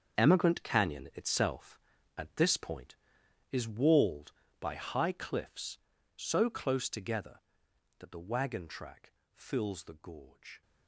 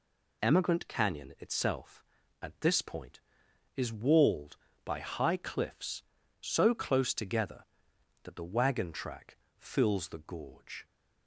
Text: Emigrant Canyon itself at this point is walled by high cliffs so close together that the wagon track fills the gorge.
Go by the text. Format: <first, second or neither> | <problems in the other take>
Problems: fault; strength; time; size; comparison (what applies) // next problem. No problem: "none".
second | gets quieter; strong; throughout; 13 dB // pauses between "track" and "fills"; slight; at 9.1 s; 0.22 s long; slight in the second